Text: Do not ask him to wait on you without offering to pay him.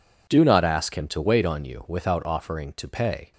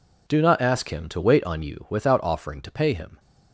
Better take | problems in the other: second | stops before "him"; at 3.3 s

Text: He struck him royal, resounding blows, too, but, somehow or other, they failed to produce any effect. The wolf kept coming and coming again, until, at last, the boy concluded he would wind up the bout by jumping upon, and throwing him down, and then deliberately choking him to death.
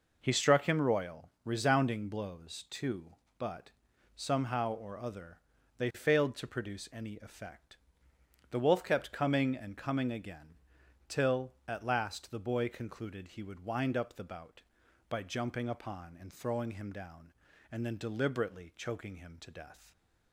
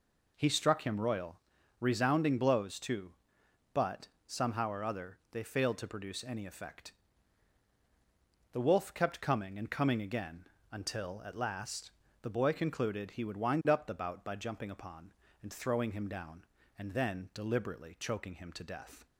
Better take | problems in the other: second | says "till" for "until"; at 11.0 s

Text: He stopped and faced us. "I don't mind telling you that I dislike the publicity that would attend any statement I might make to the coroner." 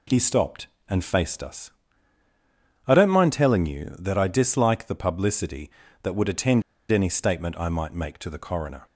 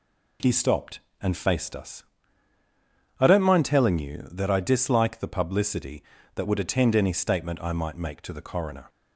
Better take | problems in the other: second | pauses between "attend" and "any"; slight; at 6.6 s; 0.29 s long

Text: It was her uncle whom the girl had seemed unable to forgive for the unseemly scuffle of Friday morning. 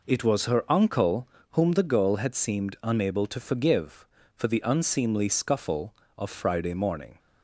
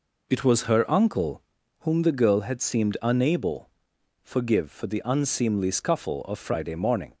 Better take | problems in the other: first | pauses between "uncle" and "whom"; at 1.4 s; 0.38 s long; slight in the first // skips "to"; at 3.9 s

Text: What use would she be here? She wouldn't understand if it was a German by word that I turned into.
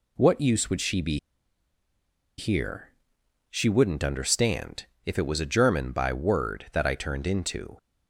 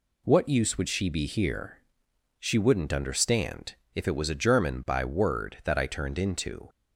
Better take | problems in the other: second | pauses between "be" and "here"; at 1.1 s; 1.1 s long // pauses between "understand" and "if"; slight; at 4.8 s; 0.20 s long; slight in the second

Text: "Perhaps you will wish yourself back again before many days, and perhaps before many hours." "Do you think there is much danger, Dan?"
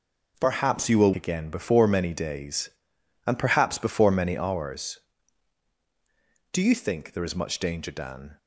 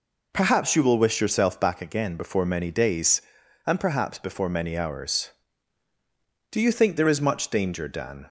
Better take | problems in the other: second | skips "wish yourself back"; at 1.1 s

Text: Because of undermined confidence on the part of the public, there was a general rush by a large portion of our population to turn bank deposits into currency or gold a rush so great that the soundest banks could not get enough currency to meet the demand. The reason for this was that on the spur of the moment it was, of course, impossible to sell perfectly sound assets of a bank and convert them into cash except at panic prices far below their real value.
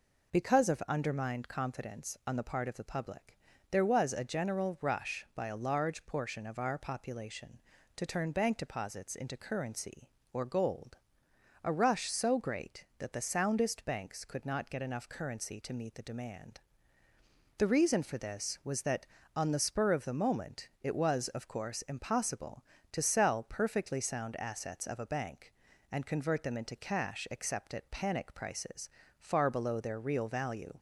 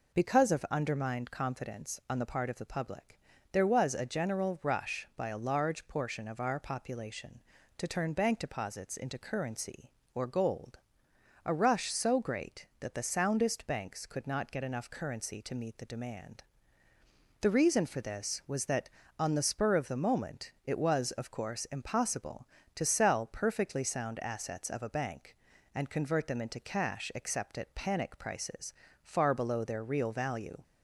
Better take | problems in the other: neither | pauses between "gold" and "a"; noticeable; the same in both // pauses between "prices" and "far"; slight; the same in both

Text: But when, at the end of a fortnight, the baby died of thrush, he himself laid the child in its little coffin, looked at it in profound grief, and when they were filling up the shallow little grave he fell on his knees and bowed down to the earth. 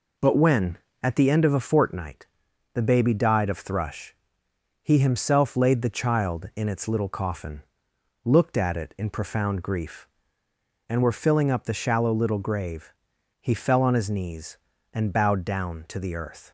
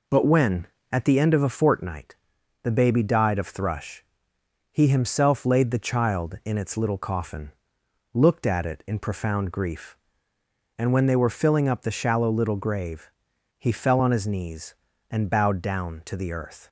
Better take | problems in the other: second | skips "when they"; at 11.0 s // pauses between "grave" and "he"; noticeable; at 12.9 s; 0.48 s long; noticeable in the second

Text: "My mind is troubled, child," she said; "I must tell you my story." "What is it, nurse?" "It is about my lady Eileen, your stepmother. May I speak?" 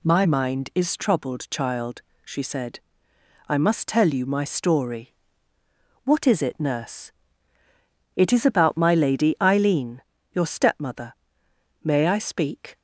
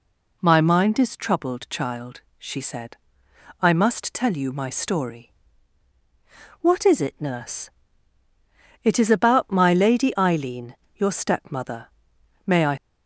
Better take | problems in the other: first | stops before "speak"; at 12.7 s

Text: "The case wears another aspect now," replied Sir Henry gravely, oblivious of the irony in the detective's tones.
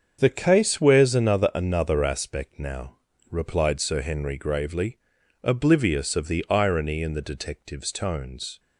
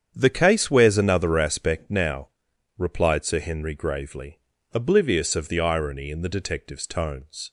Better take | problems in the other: second | starts louder than the rest; until 1.2 s; 7 dB; strong in the second // says "another" twice; at 1.5 s

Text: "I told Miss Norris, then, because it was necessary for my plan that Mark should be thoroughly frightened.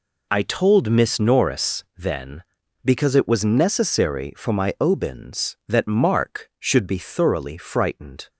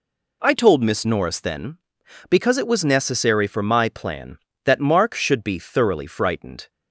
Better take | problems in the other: second | says "obins" for "plan"; at 4.7 s

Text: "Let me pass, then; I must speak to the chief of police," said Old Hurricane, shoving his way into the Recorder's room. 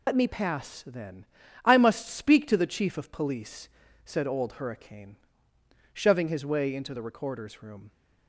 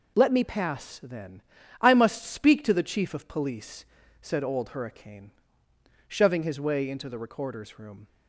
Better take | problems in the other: second | loses the start of "Let"; at 0.0 s; 80 ms

